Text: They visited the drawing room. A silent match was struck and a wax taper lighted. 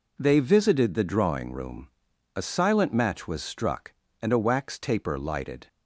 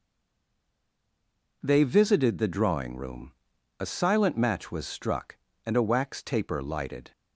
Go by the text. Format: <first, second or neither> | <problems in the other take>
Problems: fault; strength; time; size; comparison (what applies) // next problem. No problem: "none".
first | stays silent before the first word; noticeable; until 1.6 s; 1.6 s long